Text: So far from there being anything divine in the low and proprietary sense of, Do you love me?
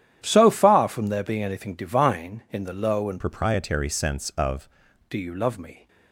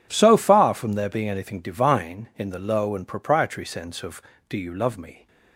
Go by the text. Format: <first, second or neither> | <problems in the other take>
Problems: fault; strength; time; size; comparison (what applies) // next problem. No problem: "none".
second | starts louder than the rest; strong; until 1.2 s; 10.5 dB // changes voice from "proprietary" to "of"; from 3.2 to 4.6 s; 1.4 s long